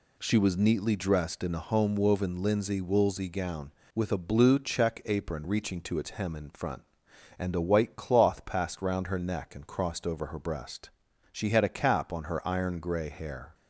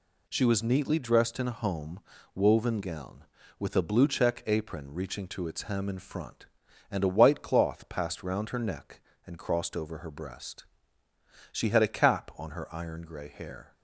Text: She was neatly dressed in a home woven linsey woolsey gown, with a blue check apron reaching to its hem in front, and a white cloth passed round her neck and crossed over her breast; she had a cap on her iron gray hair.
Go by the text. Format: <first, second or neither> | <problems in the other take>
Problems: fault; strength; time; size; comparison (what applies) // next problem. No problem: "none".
first | pauses between "home" and "woven"; slight; at 2.0 s; 0.34 s long // skips "linsey woolsey"; at 2.8 s